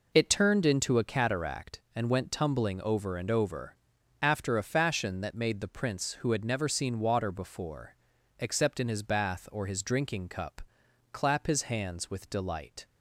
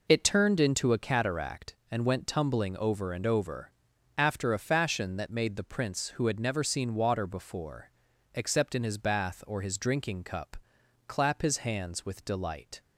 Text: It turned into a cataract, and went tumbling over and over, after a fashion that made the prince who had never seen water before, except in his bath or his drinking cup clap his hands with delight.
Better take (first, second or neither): neither